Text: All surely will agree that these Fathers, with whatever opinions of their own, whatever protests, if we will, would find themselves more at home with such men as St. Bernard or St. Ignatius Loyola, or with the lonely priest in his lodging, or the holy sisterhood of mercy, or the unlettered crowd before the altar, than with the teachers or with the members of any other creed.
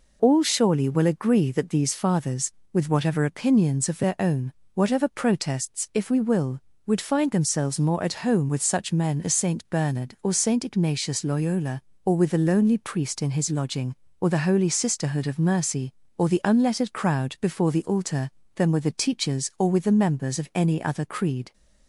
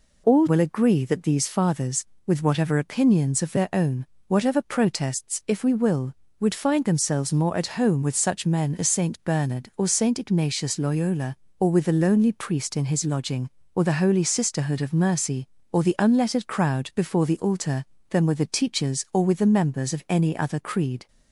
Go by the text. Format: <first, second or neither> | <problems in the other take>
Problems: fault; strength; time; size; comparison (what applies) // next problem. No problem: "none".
first | skips "surely"; at 0.4 s